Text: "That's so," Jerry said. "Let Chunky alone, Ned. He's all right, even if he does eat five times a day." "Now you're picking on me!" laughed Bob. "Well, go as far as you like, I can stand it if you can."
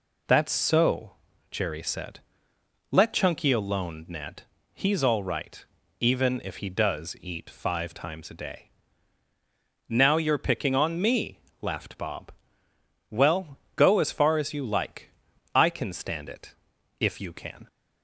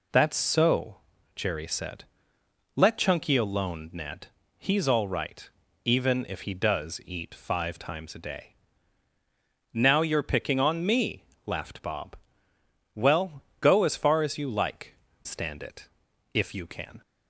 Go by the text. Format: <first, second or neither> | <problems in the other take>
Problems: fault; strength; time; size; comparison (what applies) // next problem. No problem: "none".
first | skips "I can"; at 15.0 s // pauses between "it" and "if"; noticeable; at 15.8 s; 0.46 s long; noticeable in the first